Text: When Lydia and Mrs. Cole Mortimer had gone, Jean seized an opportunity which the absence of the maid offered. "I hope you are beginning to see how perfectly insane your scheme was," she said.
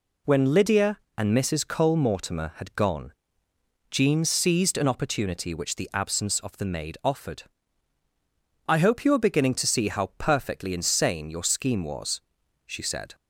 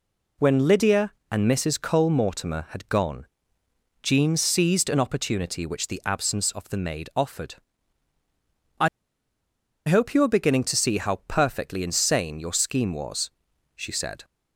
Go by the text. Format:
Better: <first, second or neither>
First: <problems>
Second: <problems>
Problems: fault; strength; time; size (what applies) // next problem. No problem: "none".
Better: first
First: none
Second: pauses between "I" and "hope"; at 8.8 s; 1.0 s long